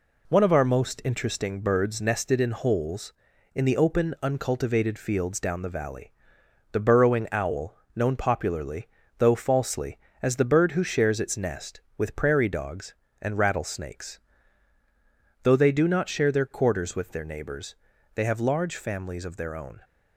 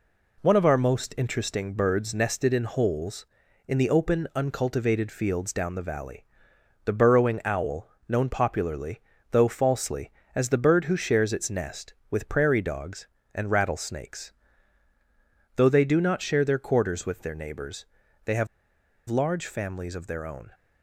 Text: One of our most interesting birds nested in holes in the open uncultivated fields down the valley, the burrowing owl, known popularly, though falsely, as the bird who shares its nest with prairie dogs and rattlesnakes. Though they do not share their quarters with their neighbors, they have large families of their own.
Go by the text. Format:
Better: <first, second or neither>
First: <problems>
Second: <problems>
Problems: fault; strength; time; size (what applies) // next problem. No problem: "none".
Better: first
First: none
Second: pauses between "have" and "large"; noticeable; at 18.4 s; 0.61 s long